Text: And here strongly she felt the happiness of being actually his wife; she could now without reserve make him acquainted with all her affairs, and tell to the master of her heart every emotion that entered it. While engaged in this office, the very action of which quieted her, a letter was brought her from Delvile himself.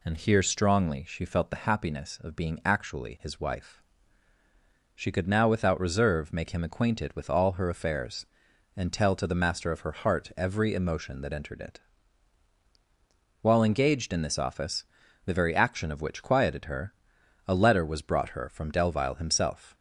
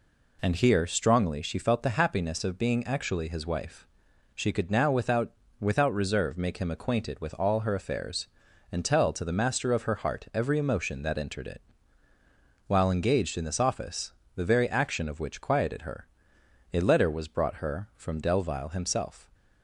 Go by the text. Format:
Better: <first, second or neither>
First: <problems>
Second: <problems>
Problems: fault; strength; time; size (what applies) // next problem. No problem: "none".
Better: first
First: none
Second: says "without" twice; at 5.5 s